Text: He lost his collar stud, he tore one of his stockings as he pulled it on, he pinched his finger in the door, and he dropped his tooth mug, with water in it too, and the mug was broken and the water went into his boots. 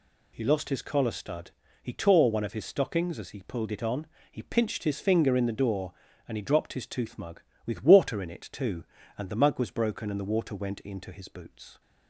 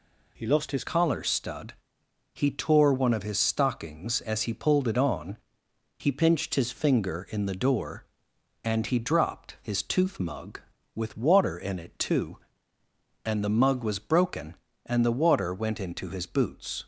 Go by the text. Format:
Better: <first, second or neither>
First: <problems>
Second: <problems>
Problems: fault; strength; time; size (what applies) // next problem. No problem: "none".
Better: first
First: none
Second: changes voice at "collar"; from 0.8 s on; 16.0 s long